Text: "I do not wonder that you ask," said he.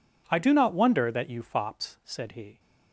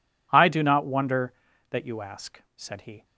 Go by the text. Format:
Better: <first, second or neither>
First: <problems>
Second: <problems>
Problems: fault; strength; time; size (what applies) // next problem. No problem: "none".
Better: second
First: says "fops" for "ask"; at 1.4 s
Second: none